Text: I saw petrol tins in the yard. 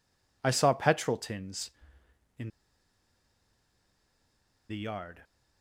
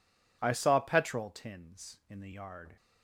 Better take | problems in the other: second | pauses between "in" and "the"; strong; at 2.4 s; 2.1 s long

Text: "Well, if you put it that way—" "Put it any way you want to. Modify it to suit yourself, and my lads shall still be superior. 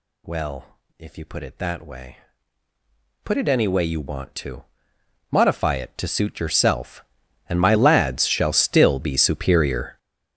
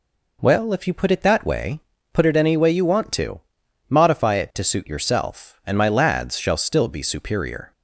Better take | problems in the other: second | gets louder; strong; throughout; 15 dB

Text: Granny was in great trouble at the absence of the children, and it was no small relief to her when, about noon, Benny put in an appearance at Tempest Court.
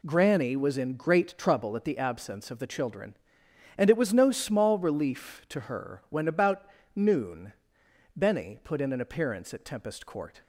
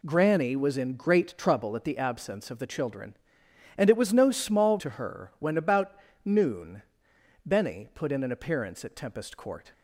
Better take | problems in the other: first | skips "relief"; at 4.7 s // pauses between "about" and "noon"; slight; at 5.9 s; 0.30 s long; slight in the first

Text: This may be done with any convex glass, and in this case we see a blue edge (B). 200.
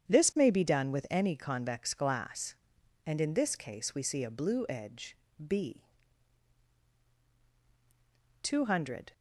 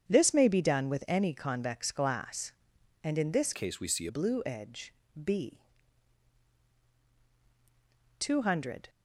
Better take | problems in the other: first | starts louder than the rest; strong; until 1.1 s; 8 dB; strong in the first // changes voice from "case" to "a"; from 3.5 to 4.0 s; 0.5 s long

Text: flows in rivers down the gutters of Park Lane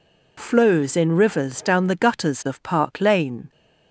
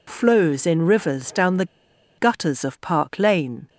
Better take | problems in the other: first | pauses between "the" and "gutters"; noticeable; at 1.6 s; 0.53 s long

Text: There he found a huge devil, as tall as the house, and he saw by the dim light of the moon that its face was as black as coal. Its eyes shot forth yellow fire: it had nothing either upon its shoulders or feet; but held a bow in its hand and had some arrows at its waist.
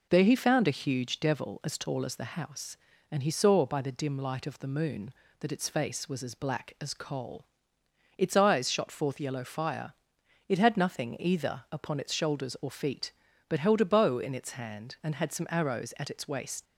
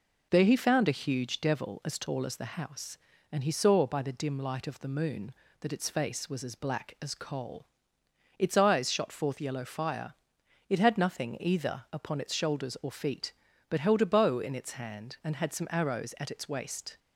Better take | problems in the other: second | leaves "waist" unfinished; at 16.6 s; 120 ms

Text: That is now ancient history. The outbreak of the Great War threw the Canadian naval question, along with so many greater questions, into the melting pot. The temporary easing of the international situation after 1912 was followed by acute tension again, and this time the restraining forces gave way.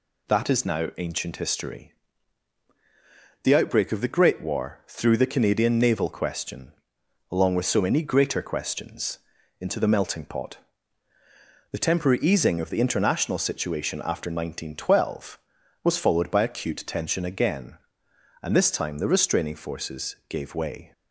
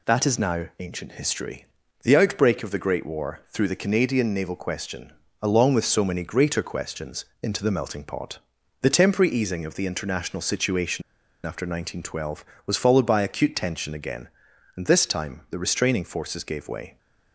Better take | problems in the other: first | pauses between "situation" and "after"; at 11.0 s; 0.43 s long

